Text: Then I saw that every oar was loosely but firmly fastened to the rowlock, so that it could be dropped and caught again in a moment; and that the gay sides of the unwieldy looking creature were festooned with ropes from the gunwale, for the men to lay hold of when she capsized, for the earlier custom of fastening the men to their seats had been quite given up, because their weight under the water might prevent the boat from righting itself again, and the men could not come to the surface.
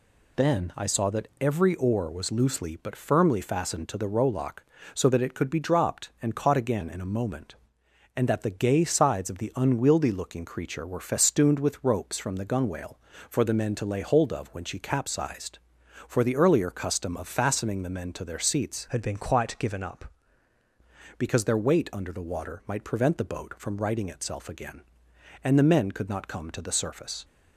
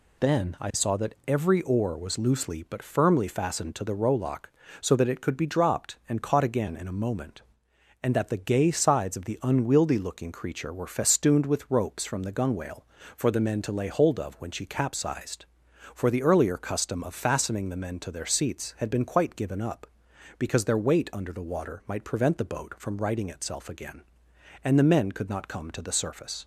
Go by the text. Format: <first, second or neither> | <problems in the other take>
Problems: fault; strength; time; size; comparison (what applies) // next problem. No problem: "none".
second | changes voice from "had" to "up"; from 18.8 to 20.0 s; 1.2 s long